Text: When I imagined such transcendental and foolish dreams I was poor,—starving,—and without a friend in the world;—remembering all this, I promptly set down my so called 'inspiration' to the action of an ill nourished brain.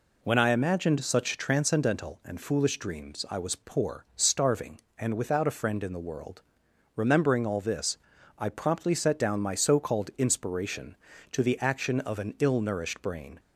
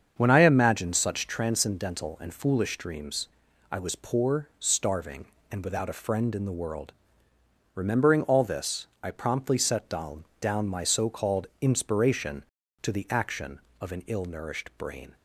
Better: first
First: none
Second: starts louder than the rest; strong; until 1.1 s; 7 dB // pauses between "dreams" and "I"; at 3.2 s; 0.42 s long // says "down" twice; at 10.3 s

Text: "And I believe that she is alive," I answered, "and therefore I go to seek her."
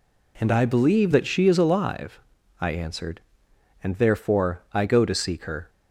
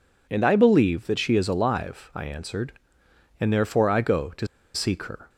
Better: first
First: none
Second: pauses between "to" and "seek"; slight; at 4.4 s; 0.27 s long

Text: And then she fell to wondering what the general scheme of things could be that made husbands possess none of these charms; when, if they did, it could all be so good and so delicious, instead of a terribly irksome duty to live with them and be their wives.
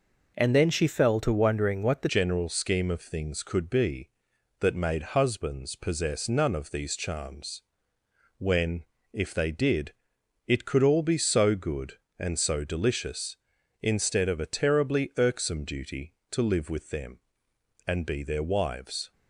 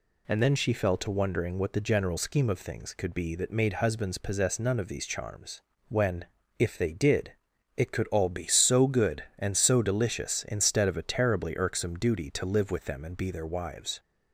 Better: second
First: changes voice at "general"; from 2.0 s on; 17.1 s long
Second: none

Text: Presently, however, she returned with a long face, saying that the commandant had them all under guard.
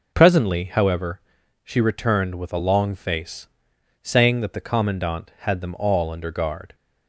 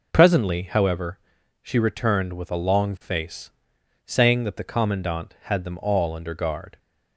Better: neither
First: none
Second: none

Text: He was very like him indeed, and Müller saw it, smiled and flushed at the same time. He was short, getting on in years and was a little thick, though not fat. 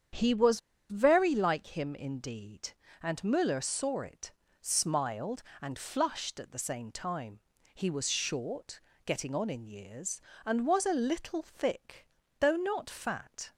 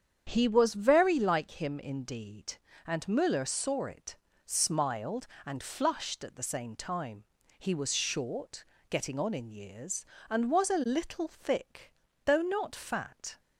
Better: second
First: starts louder than the rest; strong; until 1.4 s; 8 dB // pauses between "was" and "very"; slight; at 0.5 s; 0.29 s long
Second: starts louder than the rest; strong; until 1.2 s; 8 dB

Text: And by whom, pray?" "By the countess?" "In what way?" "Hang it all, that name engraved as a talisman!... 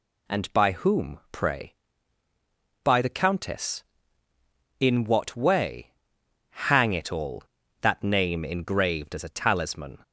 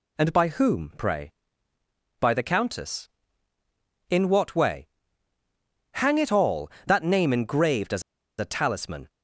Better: first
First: none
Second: pauses between "as" and "a"; at 8.0 s; 0.37 s long

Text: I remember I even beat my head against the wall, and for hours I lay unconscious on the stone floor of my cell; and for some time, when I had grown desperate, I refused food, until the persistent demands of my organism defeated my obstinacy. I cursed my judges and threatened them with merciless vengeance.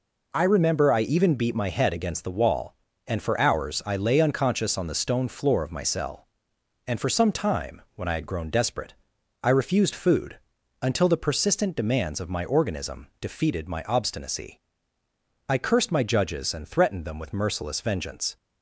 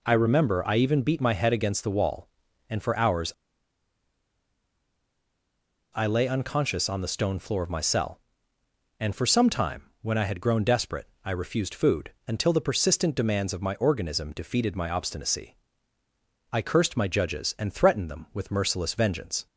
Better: first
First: none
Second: pauses between "hours" and "I"; strong; at 3.3 s; 2.6 s long

